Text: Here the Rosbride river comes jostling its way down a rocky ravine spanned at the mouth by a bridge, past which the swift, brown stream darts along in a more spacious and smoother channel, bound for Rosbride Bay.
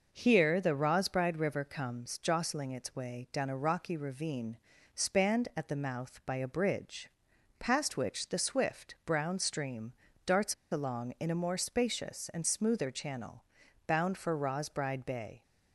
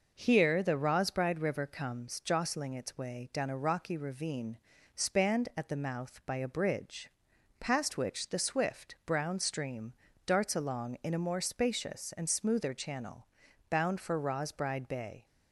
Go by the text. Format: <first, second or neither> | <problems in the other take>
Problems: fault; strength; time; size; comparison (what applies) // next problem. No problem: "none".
second | pauses between "ravine" and "spanned"; slight; at 4.5 s; 0.36 s long; slight in the second // pauses between "stream" and "darts"; slight; at 9.9 s; 0.32 s long; slight in the second // pauses between "darts" and "along"; slight; at 10.5 s; 0.18 s long